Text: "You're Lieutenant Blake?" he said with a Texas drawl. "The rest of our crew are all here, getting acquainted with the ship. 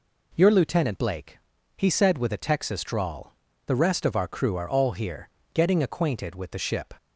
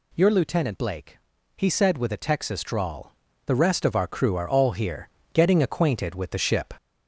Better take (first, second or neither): first